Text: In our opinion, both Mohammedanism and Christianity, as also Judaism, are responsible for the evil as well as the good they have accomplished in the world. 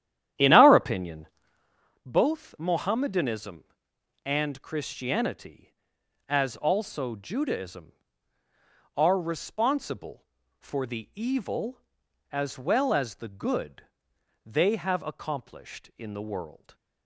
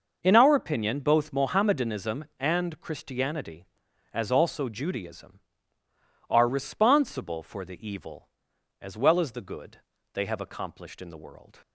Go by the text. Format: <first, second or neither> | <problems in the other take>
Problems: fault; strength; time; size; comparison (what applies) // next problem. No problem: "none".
second | starts louder than the rest; strong; until 1.9 s; 11 dB // pauses between "good" and "they"; noticeable; at 13.8 s; 0.60 s long; slight in the second